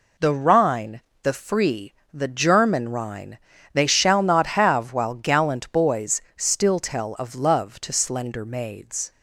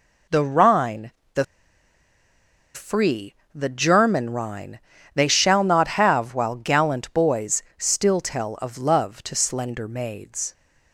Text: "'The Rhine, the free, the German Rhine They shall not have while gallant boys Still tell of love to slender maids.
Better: first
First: pauses between "Rhine" and "They"; slight; at 3.3 s; 0.36 s long // pauses between "boys" and "Still"; slight; at 6.2 s; 0.16 s long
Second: pauses between "the" and "free"; strong; at 1.4 s; 1.3 s long // pauses between "Rhine" and "They"; slight; at 4.7 s; 0.36 s long // pauses between "boys" and "Still"; slight; at 7.6 s; 0.16 s long

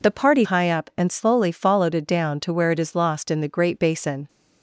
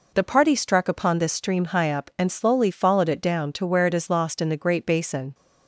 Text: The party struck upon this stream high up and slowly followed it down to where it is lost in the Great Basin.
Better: second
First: skips "struck upon this stream"; at 0.4 s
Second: none

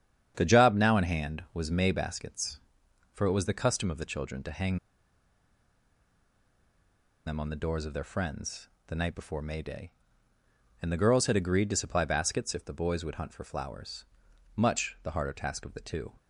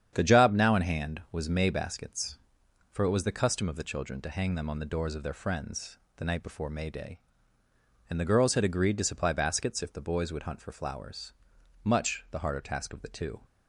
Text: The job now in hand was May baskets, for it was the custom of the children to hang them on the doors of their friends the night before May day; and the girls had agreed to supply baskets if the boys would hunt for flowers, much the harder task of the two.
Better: second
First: starts louder than the rest; strong; until 1.3 s; 8.5 dB // pauses between "hang" and "them"; strong; at 4.7 s; 2.5 s long // pauses between "friends" and "the"; slight; at 8.6 s; 0.20 s long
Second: starts louder than the rest; strong; until 1.1 s; 8.5 dB // pauses between "friends" and "the"; slight; at 5.9 s; 0.20 s long

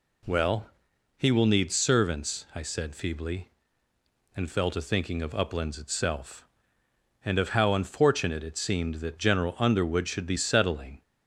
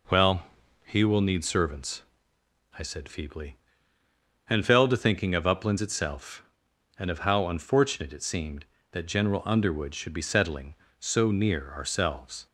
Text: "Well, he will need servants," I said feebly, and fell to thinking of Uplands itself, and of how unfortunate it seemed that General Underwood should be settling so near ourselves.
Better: second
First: stops before "so near ourselves"; at 11.0 s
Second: none

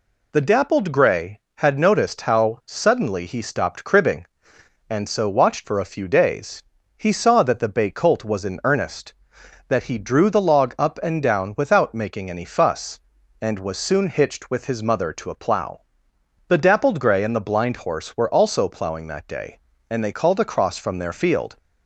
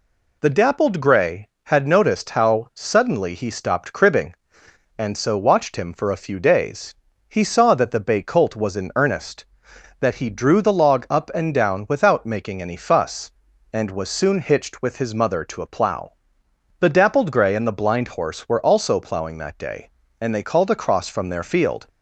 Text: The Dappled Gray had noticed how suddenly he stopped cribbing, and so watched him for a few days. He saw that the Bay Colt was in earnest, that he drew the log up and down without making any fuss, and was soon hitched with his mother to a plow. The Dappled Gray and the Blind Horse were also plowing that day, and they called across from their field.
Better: second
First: skips "him"; at 5.6 s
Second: none

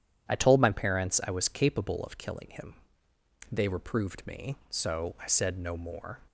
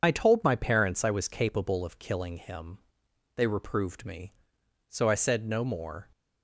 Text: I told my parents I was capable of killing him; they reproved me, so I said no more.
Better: first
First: none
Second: loses the start of "I"; at 0.0 s; 40 ms

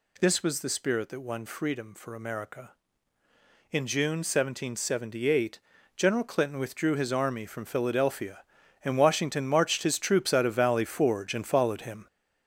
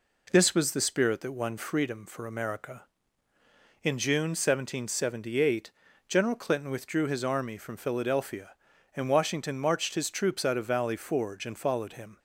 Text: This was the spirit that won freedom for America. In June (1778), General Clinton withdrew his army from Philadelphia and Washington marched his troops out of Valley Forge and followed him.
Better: second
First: gets louder; throughout; 6.5 dB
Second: none

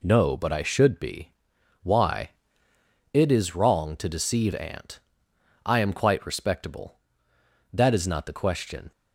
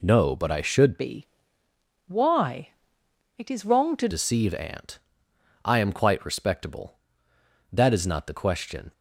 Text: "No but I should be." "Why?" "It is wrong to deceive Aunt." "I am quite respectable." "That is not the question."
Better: first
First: none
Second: changes voice from "be" to "to"; from 0.9 to 4.0 s; 3.1 s long

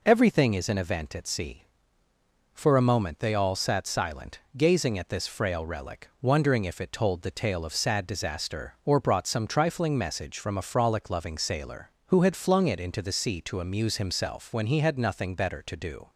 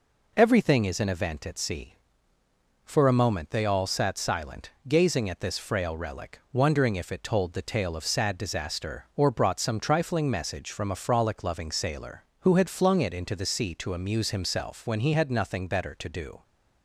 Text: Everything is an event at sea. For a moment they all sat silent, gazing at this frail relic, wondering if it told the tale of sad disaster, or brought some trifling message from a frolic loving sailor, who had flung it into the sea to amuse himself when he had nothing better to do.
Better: neither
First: none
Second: none

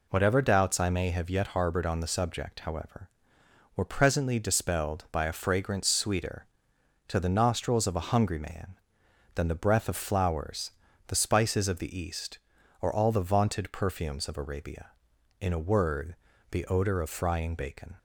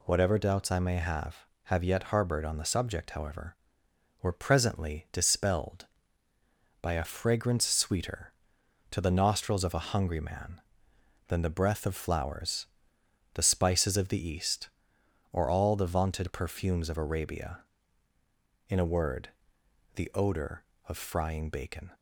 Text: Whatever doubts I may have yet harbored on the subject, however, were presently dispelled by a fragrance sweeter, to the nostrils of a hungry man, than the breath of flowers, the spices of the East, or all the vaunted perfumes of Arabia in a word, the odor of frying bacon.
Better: first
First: none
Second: says "have" twice; at 1.6 s

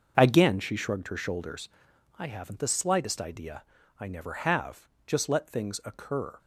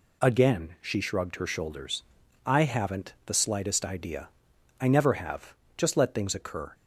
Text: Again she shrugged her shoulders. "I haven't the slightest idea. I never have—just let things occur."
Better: second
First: starts louder than the rest; until 2.0 s; 6.5 dB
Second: none

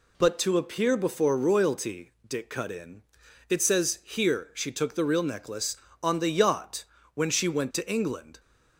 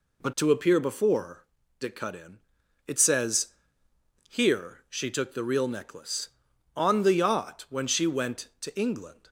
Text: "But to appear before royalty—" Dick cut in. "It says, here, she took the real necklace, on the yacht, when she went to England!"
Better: first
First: none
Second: skips "royalty"; at 1.6 s

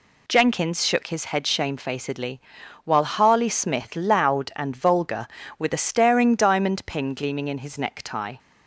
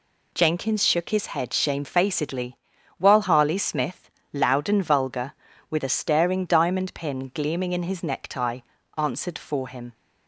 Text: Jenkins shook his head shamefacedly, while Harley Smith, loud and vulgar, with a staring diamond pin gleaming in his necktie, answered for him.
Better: second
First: stops before "answered for him"; at 8.3 s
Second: none

